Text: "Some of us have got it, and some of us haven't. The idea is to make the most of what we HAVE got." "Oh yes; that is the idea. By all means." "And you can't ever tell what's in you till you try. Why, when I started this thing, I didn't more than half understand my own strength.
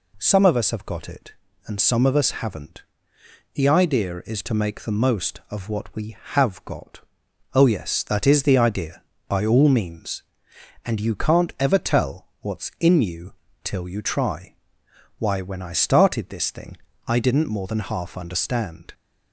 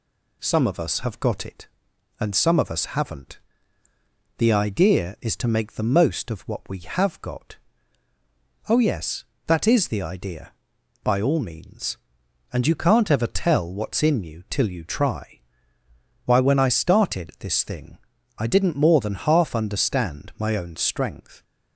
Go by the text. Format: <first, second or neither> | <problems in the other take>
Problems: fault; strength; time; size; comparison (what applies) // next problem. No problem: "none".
second | pauses between "you" and "till"; slight; at 13.3 s; 0.32 s long // stops before "my own strength"; at 18.9 s